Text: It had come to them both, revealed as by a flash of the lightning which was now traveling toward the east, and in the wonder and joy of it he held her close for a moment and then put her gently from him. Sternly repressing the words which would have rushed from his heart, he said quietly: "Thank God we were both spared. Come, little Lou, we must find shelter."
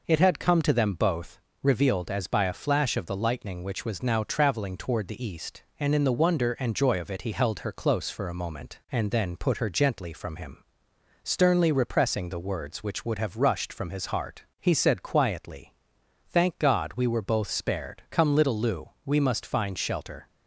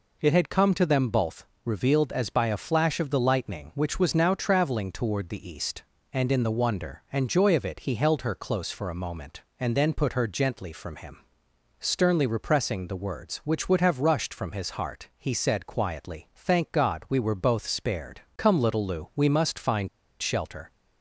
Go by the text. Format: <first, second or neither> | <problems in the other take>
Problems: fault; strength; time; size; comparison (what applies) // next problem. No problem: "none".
first | pauses between "find" and "shelter"; slight; at 19.8 s; 0.32 s long